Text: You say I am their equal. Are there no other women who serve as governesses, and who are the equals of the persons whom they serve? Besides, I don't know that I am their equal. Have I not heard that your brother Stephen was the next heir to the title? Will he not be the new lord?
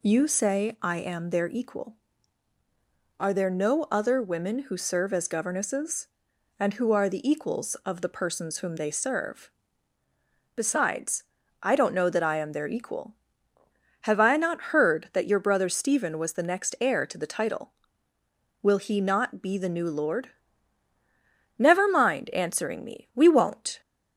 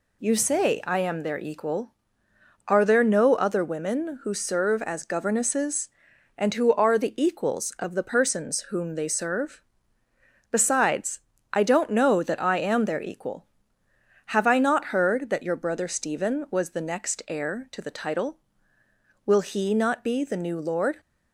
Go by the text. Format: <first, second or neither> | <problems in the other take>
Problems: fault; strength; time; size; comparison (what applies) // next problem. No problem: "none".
second | goes on to say "Never mind answering me We won't"; strong; from 21.5 s on; 2.2 s long